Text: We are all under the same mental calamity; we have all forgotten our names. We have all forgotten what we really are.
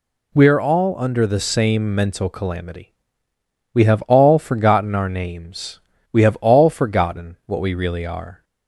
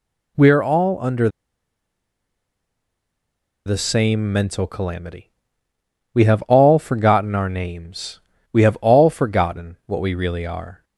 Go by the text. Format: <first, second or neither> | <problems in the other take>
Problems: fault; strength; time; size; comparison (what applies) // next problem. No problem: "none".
first | pauses between "under" and "the"; strong; at 1.2 s; 2.3 s long